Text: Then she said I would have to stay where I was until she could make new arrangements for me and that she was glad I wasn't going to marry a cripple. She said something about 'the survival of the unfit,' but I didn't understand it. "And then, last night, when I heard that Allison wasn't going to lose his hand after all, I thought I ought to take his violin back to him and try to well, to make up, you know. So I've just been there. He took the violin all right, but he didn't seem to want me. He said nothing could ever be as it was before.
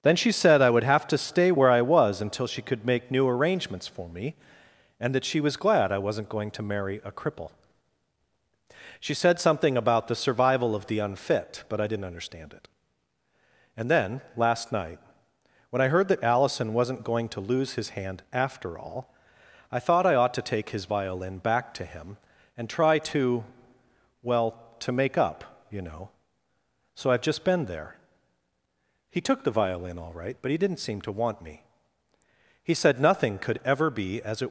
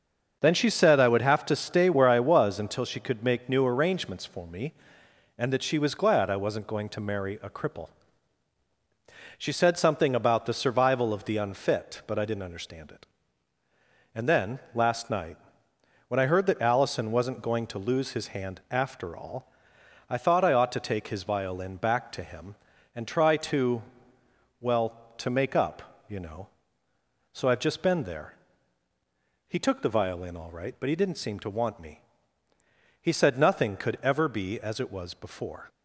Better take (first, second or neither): second